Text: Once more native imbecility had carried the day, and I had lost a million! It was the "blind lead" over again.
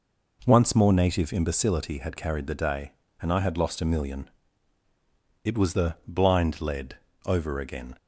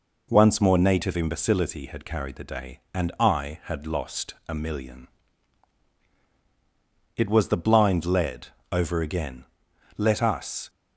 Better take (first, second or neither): first